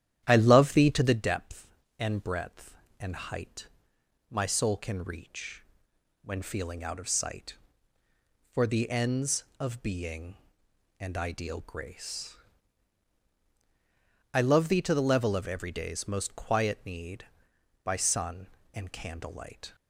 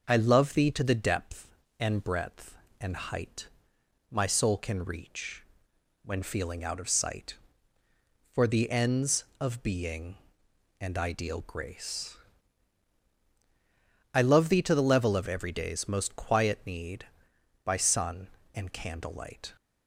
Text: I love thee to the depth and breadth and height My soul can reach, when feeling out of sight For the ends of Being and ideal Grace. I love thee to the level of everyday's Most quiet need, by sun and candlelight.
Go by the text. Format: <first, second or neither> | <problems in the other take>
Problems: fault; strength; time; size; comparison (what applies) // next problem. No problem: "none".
second | starts louder than the rest; strong; until 1.2 s; 11 dB // pauses between "height" and "My"; noticeable; at 3.6 s; 0.64 s long; noticeable in the second